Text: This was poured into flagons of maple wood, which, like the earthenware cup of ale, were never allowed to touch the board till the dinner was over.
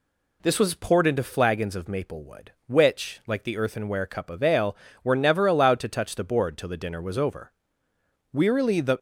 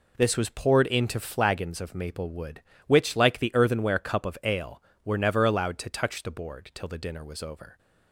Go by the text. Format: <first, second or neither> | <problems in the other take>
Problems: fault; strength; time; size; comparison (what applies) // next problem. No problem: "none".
second | goes on to say "Wearily the"; noticeable; from 8.3 s on; 0.66 s long